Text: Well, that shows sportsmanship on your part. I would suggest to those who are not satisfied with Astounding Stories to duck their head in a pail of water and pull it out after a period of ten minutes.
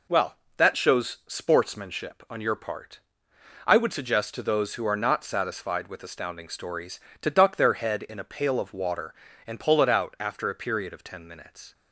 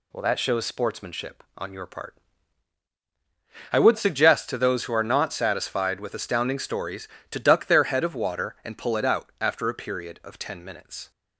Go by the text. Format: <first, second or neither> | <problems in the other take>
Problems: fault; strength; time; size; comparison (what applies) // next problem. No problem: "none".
first | skips "in a pail"; at 8.0 s